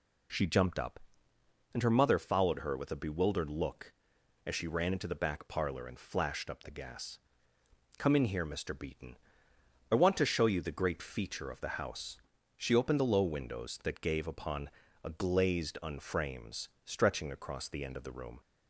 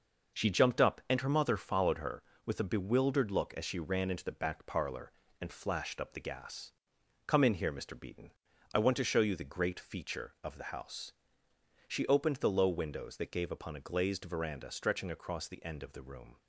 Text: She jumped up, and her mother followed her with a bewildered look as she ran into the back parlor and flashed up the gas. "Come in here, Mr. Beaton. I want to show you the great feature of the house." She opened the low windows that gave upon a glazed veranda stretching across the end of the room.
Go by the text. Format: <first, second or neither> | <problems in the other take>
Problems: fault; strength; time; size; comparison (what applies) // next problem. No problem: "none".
second | pauses between "upon" and "a"; slight; at 14.6 s; 0.34 s long // says "unframes" for "veranda"; at 15.8 s